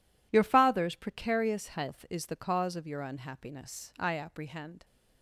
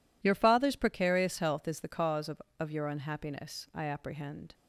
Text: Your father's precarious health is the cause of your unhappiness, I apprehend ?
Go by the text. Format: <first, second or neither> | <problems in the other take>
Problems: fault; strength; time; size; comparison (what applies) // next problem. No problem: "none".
first | says "of" twice; at 2.5 s